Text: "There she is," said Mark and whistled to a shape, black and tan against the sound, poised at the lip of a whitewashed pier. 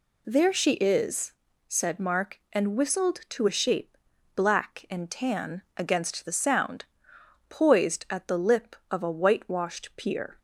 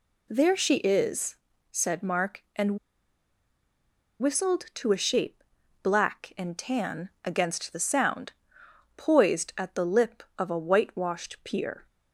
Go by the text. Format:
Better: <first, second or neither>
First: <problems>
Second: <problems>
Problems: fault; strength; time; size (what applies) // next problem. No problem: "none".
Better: first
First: none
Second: pauses between "and" and "whistled"; strong; at 2.7 s; 1.4 s long